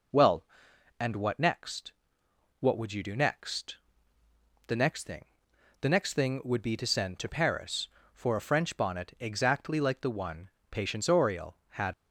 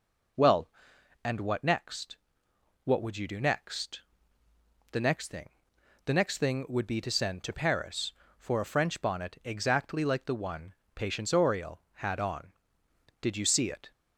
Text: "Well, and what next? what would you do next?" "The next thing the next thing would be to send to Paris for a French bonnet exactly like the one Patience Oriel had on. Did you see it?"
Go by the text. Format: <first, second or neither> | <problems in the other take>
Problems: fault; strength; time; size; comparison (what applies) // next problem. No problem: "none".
second | pauses between "thing" and "the"; noticeable; at 5.2 s; 0.56 s long; noticeable in the second // pauses between "one" and "Patience"; slight; at 10.4 s; 0.22 s long; slight in the second // stops before "on Did you see it"; at 11.9 s